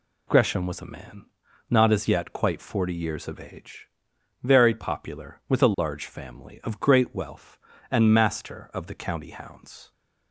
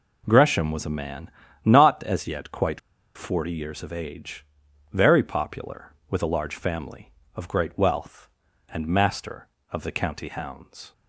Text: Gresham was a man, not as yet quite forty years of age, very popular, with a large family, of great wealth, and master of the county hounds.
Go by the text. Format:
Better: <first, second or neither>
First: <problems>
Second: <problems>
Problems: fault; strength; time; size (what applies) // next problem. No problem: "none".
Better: first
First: none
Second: pauses between "quite" and "forty"; at 2.7 s; 0.36 s long